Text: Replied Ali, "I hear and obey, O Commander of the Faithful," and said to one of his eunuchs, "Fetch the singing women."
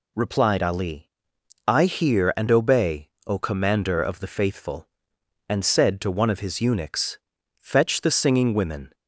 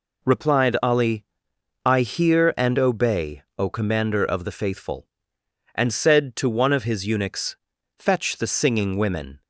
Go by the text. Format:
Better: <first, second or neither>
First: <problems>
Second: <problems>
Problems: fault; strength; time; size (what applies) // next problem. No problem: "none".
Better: neither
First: none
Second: none